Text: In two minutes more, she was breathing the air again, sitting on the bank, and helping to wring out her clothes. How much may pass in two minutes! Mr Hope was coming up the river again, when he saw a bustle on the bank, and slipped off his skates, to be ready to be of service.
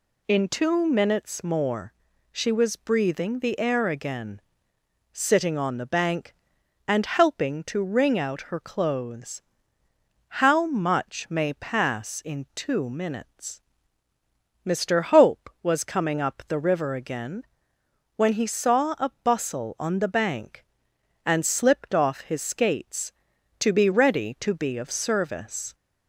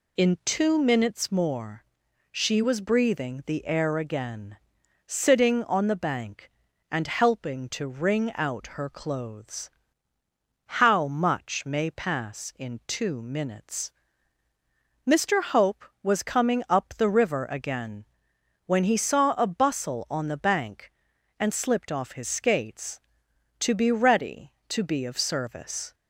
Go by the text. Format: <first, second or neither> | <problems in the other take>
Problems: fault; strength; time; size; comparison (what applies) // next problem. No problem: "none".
neither | none